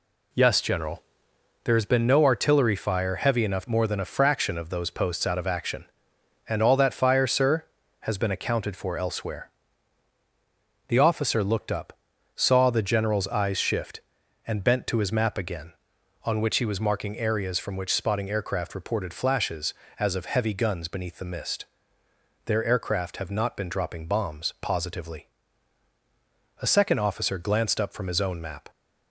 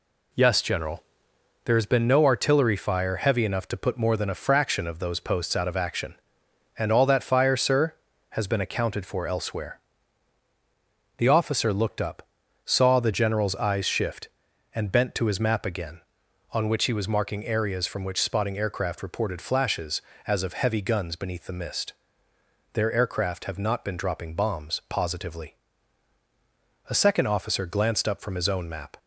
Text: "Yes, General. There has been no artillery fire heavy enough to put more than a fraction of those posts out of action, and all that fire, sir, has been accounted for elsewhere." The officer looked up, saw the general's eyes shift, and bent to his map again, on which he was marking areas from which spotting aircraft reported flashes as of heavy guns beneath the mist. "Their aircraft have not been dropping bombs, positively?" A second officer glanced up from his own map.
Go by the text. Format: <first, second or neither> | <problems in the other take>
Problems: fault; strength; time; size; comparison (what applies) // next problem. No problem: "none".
second | skips "to put"; at 3.6 s